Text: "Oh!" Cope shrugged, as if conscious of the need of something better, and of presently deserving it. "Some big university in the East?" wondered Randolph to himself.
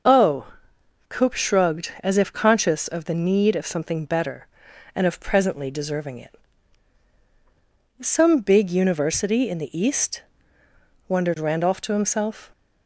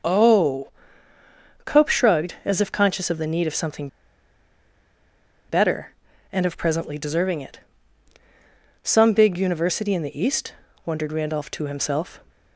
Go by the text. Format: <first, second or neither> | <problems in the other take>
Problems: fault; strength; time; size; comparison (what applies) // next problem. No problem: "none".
first | starts louder than the rest; noticeable; until 2.0 s; 6 dB // pauses between "something" and "better"; strong; at 3.8 s; 1.6 s long